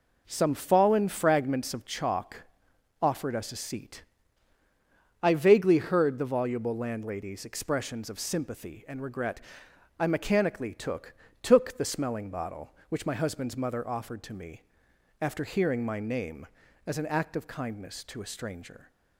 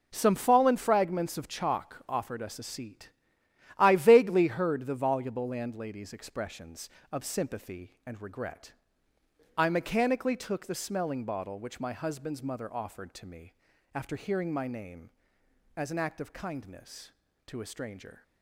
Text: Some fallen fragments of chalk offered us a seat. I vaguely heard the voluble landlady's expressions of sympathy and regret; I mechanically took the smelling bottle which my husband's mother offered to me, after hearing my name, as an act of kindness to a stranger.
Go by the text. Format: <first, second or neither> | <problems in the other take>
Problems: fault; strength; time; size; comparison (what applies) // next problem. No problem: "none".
second | pauses between "chalk" and "offered"; noticeable; at 2.4 s; 0.58 s long // says "took" twice; at 11.4 s